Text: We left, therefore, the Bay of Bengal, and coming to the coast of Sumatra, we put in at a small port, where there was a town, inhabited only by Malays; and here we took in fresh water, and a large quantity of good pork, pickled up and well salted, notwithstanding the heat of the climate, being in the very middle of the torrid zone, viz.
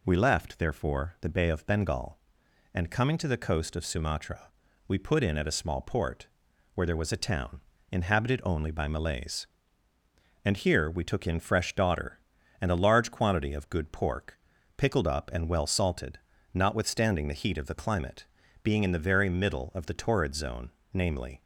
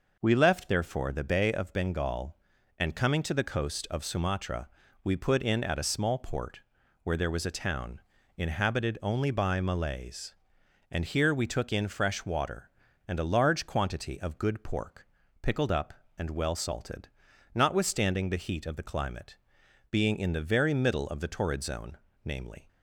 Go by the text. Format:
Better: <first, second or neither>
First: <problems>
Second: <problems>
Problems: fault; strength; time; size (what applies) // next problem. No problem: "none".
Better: second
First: says "daughter" for "water"; at 11.7 s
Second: none